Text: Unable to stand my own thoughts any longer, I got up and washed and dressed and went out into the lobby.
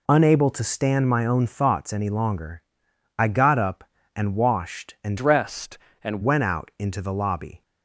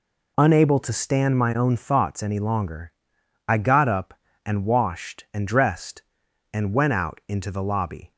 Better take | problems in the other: second | changes voice from "dressed" to "and"; from 5.1 to 6.2 s; 1.1 s long

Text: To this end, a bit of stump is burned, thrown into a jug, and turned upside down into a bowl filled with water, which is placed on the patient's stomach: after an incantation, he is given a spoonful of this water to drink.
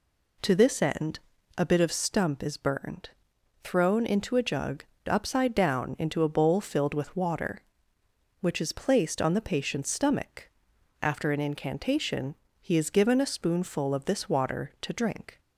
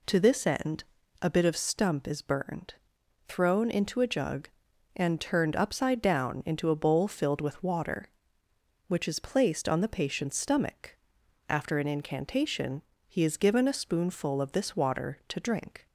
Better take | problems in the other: second | skips "and turned"; at 4.9 s

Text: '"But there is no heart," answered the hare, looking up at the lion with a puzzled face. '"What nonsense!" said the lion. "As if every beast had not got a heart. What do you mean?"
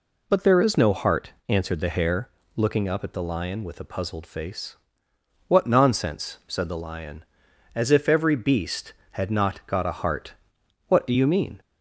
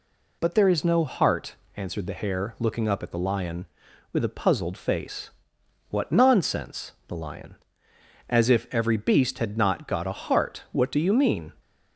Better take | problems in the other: first | skips "said"; at 7.0 s

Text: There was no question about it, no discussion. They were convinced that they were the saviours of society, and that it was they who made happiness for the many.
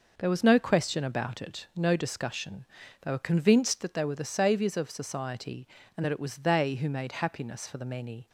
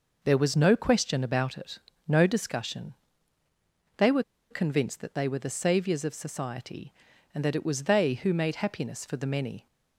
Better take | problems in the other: first | pauses between "were" and "convinced"; slight; at 4.2 s; 0.28 s long

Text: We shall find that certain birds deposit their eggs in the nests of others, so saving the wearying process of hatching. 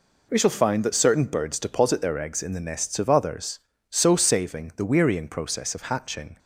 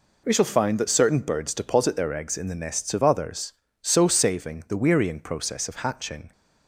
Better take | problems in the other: neither | none

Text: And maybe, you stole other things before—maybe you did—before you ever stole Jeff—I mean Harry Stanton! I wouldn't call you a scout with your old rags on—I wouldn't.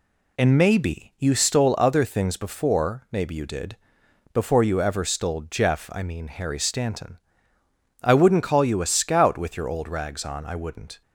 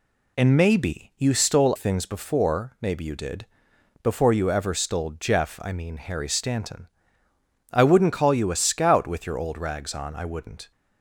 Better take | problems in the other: first | skips "other"; at 1.7 s

